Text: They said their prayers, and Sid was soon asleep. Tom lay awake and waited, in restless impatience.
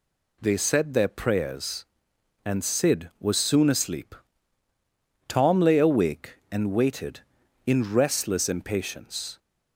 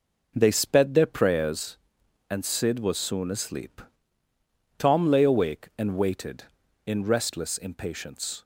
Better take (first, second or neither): first